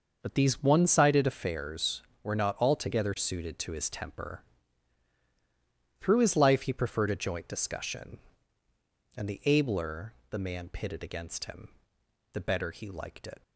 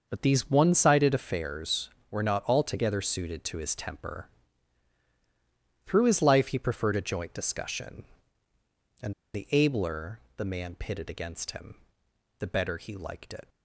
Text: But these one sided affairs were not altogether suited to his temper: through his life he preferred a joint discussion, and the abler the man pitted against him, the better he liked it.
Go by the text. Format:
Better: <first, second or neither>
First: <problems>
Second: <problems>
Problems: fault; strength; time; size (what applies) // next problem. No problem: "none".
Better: first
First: starts louder than the rest; noticeable; until 1.2 s; 6 dB // pauses between "abler" and "the"; slight; at 10.1 s; 0.18 s long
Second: starts louder than the rest; noticeable; until 1.1 s; 6 dB // pauses between "and" and "the"; slight; at 9.1 s; 0.21 s long // pauses between "abler" and "the"; slight; at 10.1 s; 0.18 s long